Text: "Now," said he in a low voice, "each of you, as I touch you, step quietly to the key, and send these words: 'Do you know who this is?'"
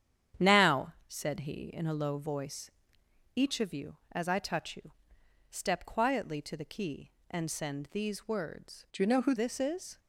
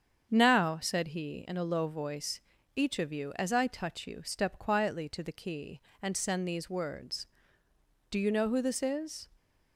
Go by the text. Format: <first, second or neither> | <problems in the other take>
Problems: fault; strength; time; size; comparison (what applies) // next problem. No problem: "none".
second | starts louder than the rest; strong; until 1.5 s; 9.5 dB; strong in the second // changes voice from "Do" to "who"; from 8.9 to 9.3 s; 0.4 s long